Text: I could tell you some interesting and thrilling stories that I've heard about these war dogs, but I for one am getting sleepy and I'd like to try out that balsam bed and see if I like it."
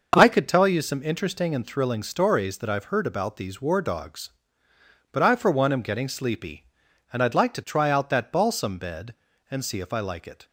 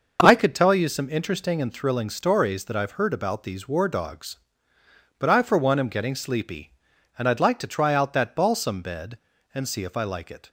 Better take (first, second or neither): neither